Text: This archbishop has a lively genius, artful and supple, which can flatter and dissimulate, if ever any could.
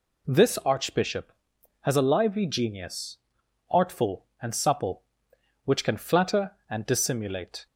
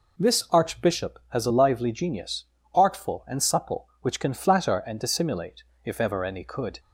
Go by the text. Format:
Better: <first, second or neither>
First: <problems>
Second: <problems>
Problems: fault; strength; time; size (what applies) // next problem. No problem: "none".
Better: second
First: stops before "if ever any could"; at 7.6 s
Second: none